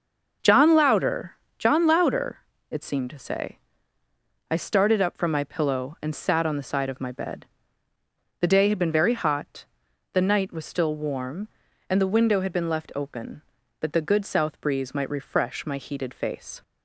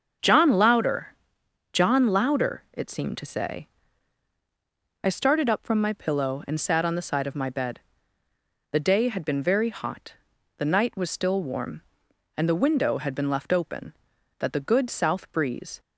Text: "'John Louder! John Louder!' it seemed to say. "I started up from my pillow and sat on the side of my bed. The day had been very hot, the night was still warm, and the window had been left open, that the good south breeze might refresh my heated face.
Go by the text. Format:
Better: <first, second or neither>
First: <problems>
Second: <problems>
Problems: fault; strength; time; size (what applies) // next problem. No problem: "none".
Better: first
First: starts louder than the rest; until 1.6 s; 6 dB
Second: starts louder than the rest; until 1.7 s; 6.5 dB // stops before "might refresh my heated face"; at 15.7 s